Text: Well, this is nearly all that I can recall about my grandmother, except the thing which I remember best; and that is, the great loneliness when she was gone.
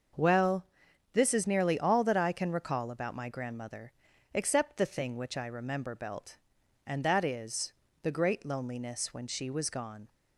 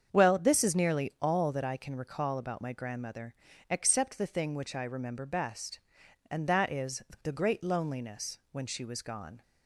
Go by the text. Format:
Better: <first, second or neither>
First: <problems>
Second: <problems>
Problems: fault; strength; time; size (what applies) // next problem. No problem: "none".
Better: second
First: starts louder than the rest; until 1.6 s; 6 dB // says "belt" for "best"; at 5.9 s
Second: starts louder than the rest; strong; until 1.1 s; 7.5 dB